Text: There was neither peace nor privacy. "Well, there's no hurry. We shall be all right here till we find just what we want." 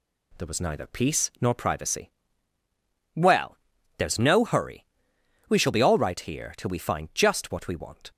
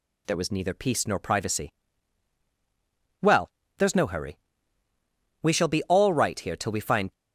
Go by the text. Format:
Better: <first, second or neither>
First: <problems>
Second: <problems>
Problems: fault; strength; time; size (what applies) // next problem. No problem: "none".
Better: first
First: none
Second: stops before "just what we want"; at 7.1 s